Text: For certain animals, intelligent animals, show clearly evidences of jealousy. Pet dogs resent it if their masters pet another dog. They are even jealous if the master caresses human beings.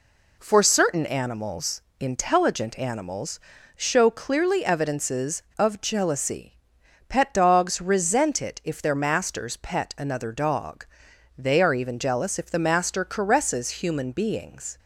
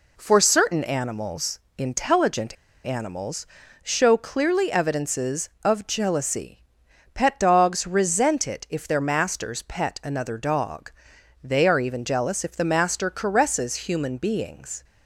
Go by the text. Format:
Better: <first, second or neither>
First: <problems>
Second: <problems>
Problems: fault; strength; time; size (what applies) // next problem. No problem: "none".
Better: first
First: none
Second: pauses between "intelligent" and "animals"; slight; at 2.5 s; 0.30 s long